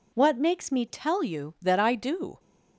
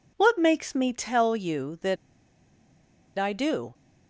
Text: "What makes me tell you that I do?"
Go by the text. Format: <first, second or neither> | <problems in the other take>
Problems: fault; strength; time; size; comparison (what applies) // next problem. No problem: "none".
first | pauses between "that" and "I"; at 1.9 s; 1.2 s long